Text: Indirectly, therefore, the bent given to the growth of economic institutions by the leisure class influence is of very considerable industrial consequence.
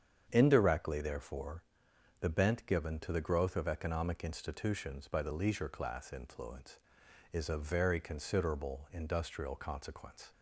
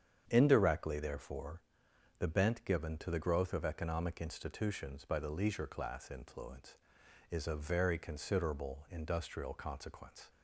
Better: neither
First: starts louder than the rest; strong; until 1.3 s; 8 dB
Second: starts louder than the rest; strong; until 1.3 s; 8 dB

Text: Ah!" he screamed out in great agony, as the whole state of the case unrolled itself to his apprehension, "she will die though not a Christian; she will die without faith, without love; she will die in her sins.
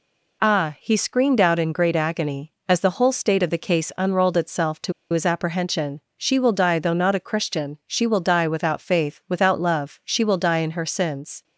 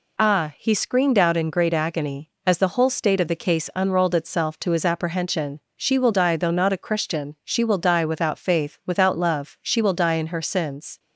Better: second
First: pauses between "to" and "his"; slight; at 4.9 s; 0.20 s long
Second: none

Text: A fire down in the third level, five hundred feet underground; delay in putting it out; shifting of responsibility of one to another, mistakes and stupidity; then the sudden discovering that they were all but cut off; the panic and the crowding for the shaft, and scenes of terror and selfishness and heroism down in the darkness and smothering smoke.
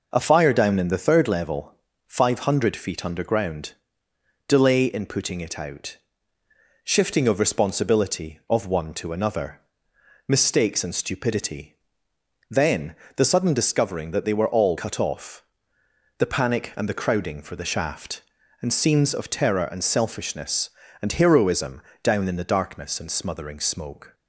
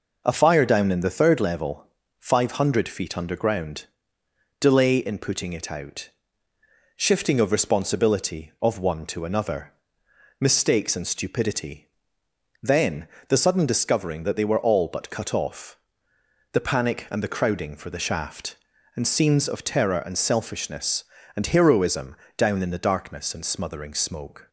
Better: second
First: pauses between "then" and "the"; slight; at 12.9 s; 0.22 s long // skips "but"; at 14.7 s // pauses between "heroism" and "down"; slight; at 21.8 s; 0.22 s long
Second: pauses between "then" and "the"; slight; at 13.0 s; 0.22 s long // pauses between "heroism" and "down"; slight; at 22.1 s; 0.22 s long

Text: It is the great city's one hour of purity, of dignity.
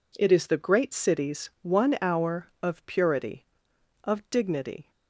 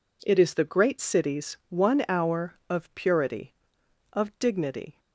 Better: neither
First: none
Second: none

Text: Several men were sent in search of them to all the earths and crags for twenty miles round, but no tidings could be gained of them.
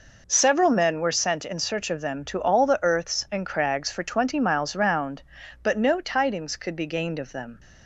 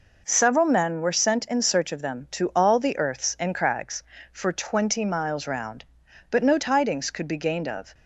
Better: first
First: none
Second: stops before "them"; at 7.9 s

